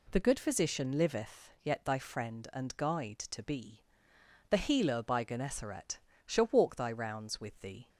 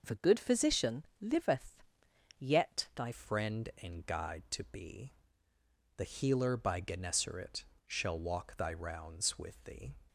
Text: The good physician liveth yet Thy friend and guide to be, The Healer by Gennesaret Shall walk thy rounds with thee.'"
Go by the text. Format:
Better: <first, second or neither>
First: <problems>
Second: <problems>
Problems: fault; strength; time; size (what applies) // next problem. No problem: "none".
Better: first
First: pauses between "Gennesaret" and "Shall"; slight; at 5.9 s; 0.28 s long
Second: pauses between "physician" and "liveth"; slight; at 1.0 s; 0.16 s long // pauses between "liveth" and "yet"; noticeable; at 1.8 s; 0.56 s long // changes voice at "friend"; from 3.1 s on; 6.8 s long // pauses between "Gennesaret" and "Shall"; slight; at 7.6 s; 0.22 s long